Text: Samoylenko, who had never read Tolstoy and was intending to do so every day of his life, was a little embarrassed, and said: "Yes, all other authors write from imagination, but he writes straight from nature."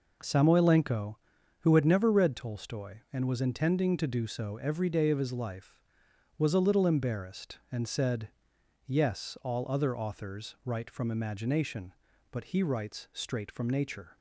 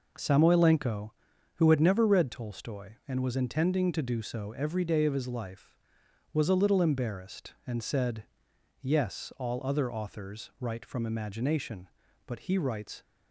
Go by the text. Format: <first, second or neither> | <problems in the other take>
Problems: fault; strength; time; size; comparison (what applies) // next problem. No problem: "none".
first | stops before "straight from nature"; at 13.0 s